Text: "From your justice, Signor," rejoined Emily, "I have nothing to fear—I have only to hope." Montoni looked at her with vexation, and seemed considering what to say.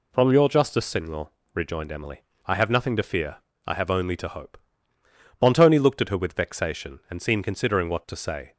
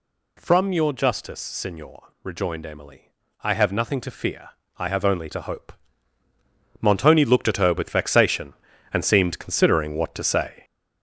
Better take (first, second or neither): first